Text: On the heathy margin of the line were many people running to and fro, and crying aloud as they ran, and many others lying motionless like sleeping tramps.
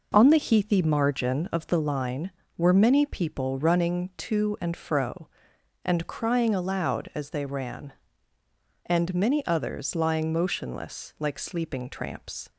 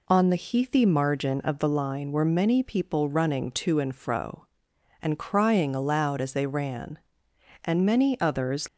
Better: first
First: none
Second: stops before "lying motionless like sleeping tramps"; at 8.6 s

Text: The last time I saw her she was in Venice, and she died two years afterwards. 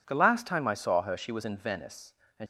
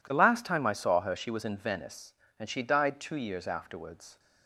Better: second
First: stops before "she died two years afterwards"; at 2.4 s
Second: none

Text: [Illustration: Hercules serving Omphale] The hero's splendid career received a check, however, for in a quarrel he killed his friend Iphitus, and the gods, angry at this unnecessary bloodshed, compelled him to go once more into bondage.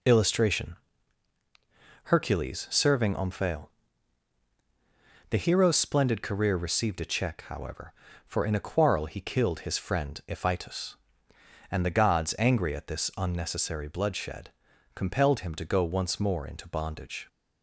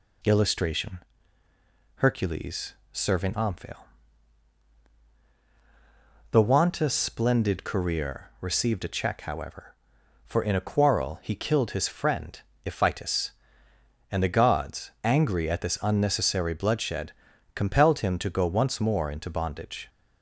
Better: first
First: pauses between "Omphale" and "The"; strong; at 3.6 s; 1.6 s long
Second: pauses between "Hercules" and "serving"; slight; at 2.7 s; 0.18 s long // pauses between "Omphale" and "The"; strong; at 3.8 s; 2.5 s long // says "wanta" for "hero's"; at 6.4 s // pauses between "friend" and "Iphitus"; slight; at 12.3 s; 0.26 s long

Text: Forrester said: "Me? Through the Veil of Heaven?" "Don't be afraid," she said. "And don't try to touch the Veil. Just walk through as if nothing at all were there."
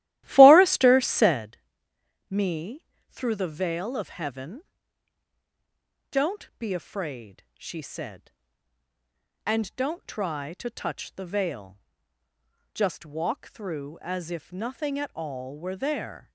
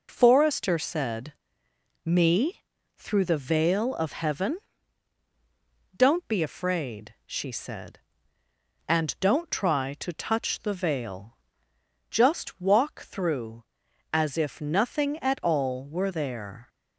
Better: second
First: starts louder than the rest; strong; until 1.5 s; 15 dB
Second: none

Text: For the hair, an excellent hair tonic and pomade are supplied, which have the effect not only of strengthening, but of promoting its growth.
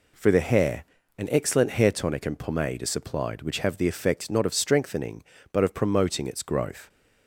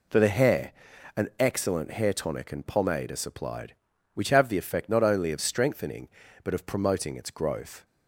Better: second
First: skips "only"; at 4.4 s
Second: none

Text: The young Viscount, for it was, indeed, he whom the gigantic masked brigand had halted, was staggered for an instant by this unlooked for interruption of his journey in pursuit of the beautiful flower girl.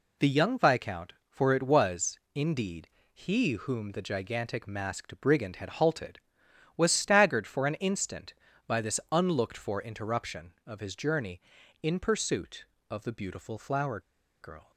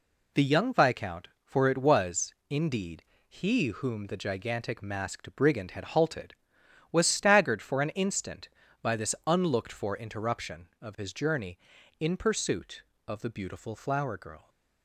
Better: second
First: pauses between "flower" and "girl"; at 13.9 s; 0.42 s long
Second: none

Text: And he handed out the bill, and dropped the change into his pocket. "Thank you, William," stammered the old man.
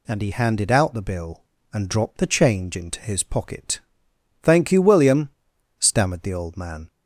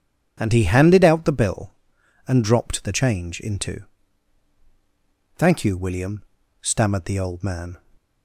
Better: first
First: none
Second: skips "his pocket"; at 4.5 s

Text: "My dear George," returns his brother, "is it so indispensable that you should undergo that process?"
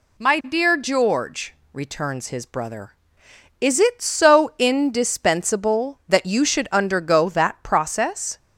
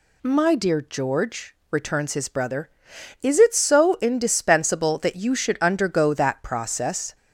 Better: neither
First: none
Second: none

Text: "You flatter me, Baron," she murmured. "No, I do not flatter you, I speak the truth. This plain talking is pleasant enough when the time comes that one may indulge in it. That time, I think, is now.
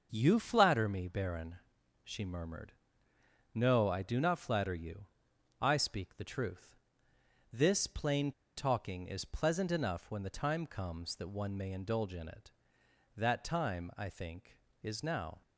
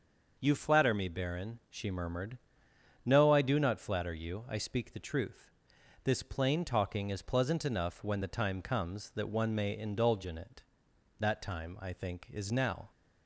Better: second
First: starts louder than the rest; until 1.1 s; 6.5 dB // pauses between "plain" and "talking"; slight; at 8.3 s; 0.25 s long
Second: starts louder than the rest; noticeable; until 1.3 s; 6 dB

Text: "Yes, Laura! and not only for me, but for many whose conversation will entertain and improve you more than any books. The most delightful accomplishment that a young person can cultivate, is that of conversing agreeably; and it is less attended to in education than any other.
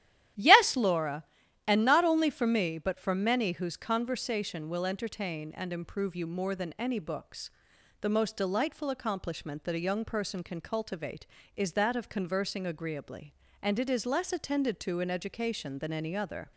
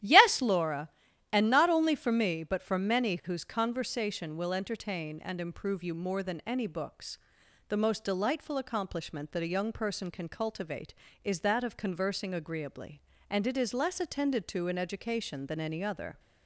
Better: neither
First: starts louder than the rest; strong; until 1.8 s; 12 dB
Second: starts louder than the rest; strong; until 1.4 s; 12 dB

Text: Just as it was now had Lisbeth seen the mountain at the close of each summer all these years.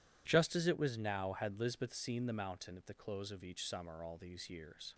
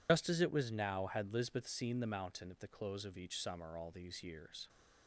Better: first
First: none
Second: loses the start of "Just"; at 0.0 s; 105 ms

